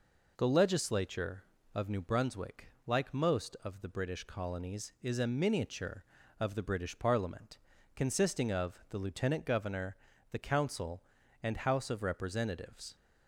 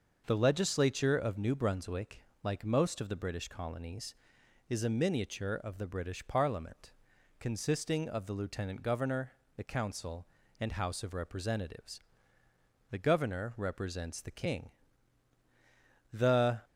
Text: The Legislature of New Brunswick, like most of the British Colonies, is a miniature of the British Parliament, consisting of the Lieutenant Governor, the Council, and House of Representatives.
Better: first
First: none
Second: starts louder than the rest; until 1.2 s; 6 dB // goes on to say "The Governor represents the King The"; strong; from 12.8 s on; 3.7 s long

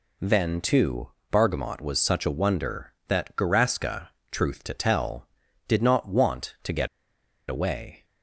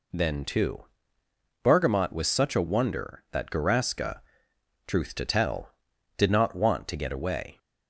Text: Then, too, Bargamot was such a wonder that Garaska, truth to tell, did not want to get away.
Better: second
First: pauses between "get" and "away"; noticeable; at 6.8 s; 0.62 s long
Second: none

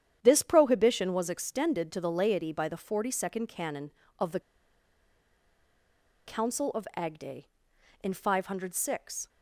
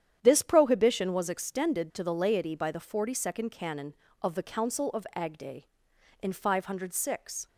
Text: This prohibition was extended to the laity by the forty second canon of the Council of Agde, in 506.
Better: second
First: starts louder than the rest; strong; until 1.2 s; 9.5 dB // pauses between "the" and "Council"; strong; at 4.4 s; 1.8 s long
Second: starts louder than the rest; strong; until 1.2 s; 9.5 dB

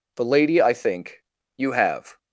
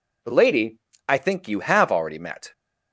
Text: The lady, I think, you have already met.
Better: second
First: stops before "already met"; at 2.1 s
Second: none

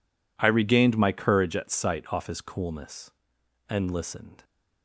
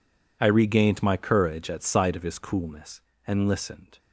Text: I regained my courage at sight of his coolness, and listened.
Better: second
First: says "off" for "of"; at 2.1 s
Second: none

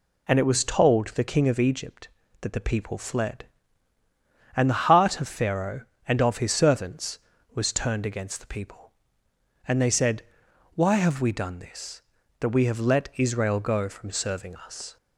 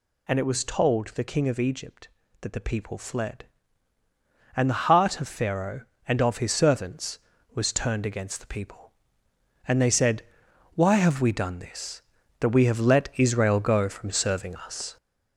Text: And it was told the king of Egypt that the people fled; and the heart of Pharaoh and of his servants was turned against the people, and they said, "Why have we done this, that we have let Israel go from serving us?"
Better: first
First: none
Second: gets louder; noticeable; throughout; 5 dB

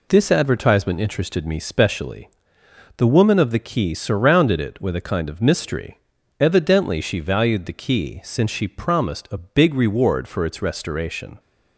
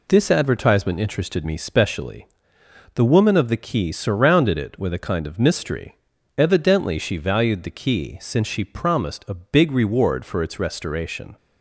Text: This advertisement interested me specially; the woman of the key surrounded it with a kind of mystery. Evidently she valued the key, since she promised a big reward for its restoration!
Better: neither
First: none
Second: none

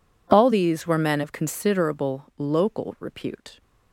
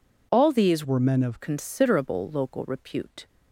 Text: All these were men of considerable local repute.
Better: first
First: none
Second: changes voice from "were" to "of"; from 0.8 to 1.3 s; 0.5 s long

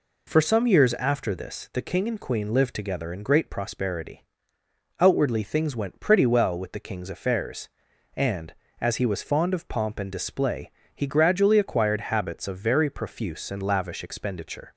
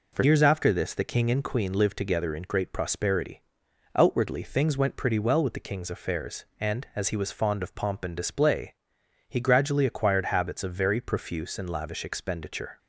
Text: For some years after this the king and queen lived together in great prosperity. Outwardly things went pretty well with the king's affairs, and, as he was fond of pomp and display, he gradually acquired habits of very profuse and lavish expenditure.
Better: first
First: none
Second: skips "some"; at 0.2 s

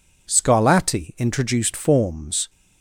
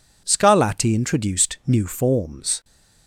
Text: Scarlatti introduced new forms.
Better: second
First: skips "new"; at 1.7 s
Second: none

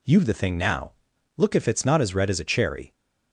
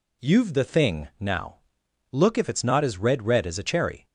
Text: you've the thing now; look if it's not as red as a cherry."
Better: first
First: none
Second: says "red" twice; at 3.2 s

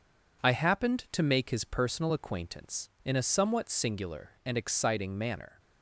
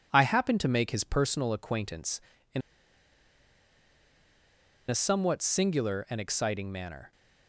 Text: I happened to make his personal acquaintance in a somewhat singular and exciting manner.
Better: first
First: none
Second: pauses between "in" and "a"; strong; at 2.6 s; 2.2 s long

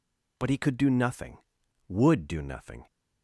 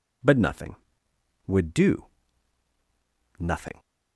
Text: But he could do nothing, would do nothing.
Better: first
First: none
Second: skips "he could do"; at 0.3 s // pauses between "do" and "nothing"; strong; at 2.0 s; 1.3 s long

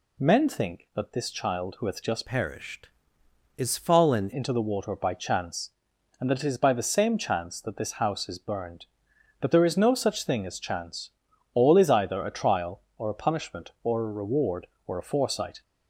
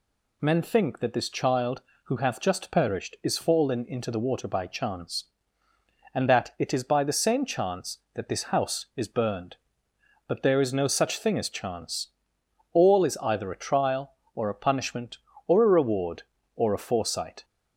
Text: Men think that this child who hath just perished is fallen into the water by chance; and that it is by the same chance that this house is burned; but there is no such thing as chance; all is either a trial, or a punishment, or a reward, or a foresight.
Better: second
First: changes voice from "perished" to "fallen"; from 2.2 to 4.2 s; 2.0 s long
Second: none

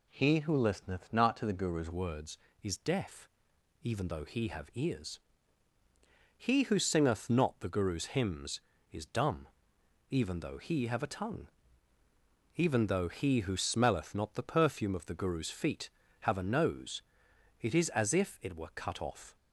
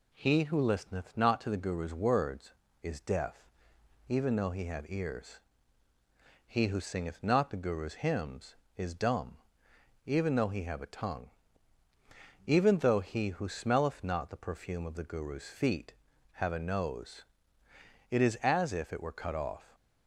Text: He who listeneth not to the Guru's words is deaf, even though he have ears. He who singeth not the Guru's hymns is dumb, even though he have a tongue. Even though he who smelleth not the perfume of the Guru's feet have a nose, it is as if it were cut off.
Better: second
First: changes voice at "words"; from 1.9 s on; 17.4 s long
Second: none

